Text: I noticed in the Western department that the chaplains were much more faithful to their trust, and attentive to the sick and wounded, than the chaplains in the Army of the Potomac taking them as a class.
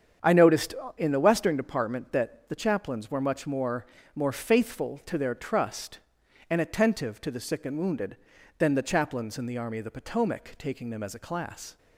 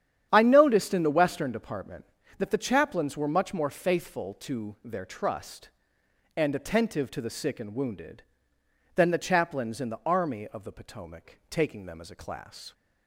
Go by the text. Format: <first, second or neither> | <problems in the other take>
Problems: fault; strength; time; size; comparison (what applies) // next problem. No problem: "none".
second | starts louder than the rest; strong; until 1.4 s; 8 dB; strong in the second // says "more" twice; at 4.1 s